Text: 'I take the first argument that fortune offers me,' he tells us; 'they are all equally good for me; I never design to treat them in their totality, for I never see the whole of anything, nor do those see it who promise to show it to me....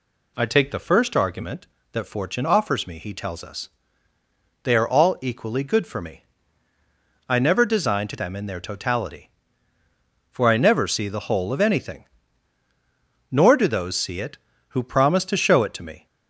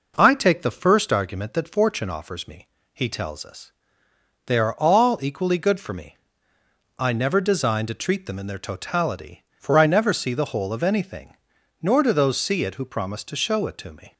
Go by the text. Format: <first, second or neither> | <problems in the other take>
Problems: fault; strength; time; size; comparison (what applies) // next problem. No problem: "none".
second | skips "treat"; at 8.1 s